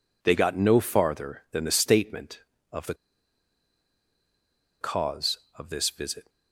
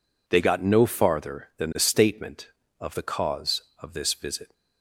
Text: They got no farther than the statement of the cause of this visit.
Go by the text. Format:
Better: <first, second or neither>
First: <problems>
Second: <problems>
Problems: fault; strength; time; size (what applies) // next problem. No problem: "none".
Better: second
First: pauses between "the" and "cause"; strong; at 2.9 s; 1.8 s long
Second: none